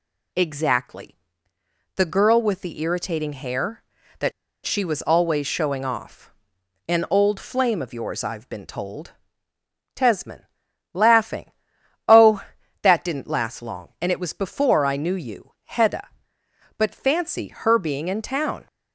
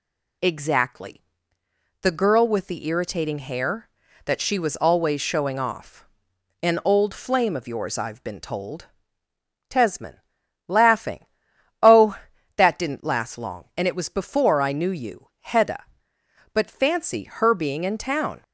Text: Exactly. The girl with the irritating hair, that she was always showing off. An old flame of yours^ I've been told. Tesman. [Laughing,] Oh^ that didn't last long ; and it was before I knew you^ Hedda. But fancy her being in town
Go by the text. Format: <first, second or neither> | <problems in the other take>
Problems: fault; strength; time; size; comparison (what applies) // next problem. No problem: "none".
second | pauses between "that" and "she"; slight; at 4.3 s; 0.34 s long